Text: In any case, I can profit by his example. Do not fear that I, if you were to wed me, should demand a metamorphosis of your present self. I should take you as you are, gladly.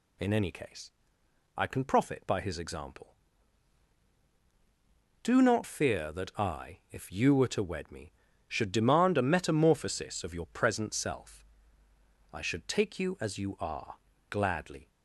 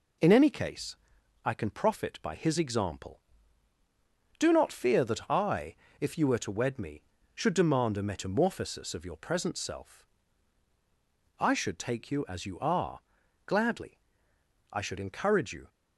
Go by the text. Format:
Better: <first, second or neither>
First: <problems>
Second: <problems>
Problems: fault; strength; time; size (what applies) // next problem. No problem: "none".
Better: first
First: none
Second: goes on to say "I should encourage you"; noticeable; from 14.7 s on; 0.96 s long